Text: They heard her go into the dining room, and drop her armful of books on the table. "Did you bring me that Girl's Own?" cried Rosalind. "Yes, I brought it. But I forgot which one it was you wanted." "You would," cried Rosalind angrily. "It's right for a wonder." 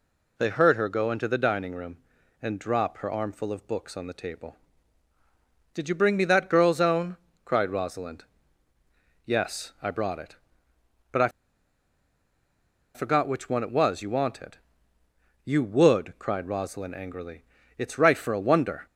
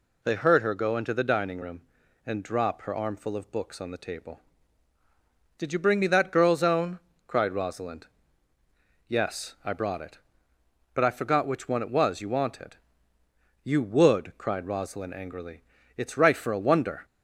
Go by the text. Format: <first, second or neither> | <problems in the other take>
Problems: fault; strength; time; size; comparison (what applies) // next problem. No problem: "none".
second | pauses between "I" and "forgot"; strong; at 11.2 s; 1.6 s long